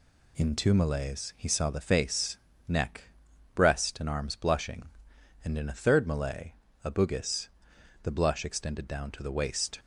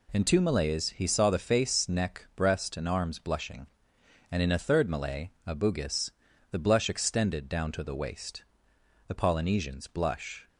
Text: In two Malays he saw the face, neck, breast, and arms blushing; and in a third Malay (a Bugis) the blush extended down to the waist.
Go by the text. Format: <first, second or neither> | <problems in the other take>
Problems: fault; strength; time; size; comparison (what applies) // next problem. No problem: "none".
first | goes on to say "The Polynesians blush"; from 9.0 s on; 1.4 s long